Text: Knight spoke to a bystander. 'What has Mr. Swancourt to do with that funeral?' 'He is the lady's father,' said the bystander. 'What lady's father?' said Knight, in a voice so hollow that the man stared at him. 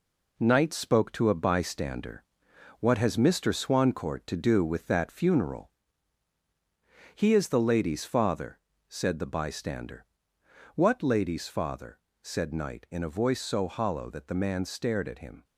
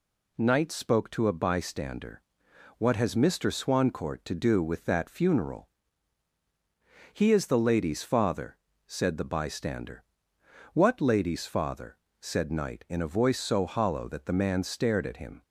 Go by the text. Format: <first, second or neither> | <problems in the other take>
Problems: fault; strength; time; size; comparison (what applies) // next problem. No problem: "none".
second | gets quieter; noticeable; throughout; 6 dB